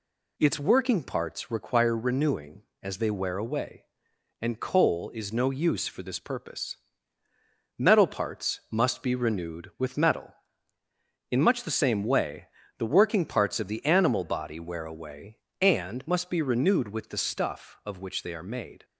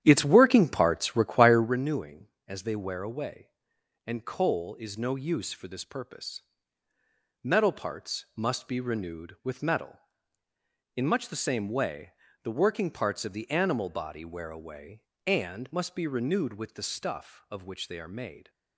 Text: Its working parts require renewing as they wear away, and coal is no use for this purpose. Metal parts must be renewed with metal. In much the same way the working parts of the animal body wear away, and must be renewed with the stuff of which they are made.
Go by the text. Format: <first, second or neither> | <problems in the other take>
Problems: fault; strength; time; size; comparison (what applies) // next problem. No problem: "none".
first | starts louder than the rest; strong; until 1.8 s; 10.5 dB // pauses between "way" and "the"; slight; at 12.1 s; 0.30 s long; slight in the first